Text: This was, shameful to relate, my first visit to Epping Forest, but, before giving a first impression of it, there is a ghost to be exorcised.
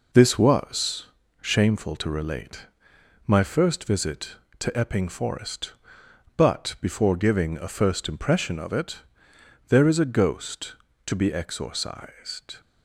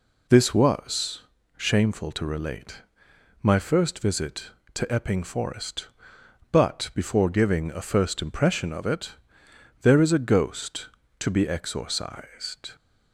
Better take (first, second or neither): second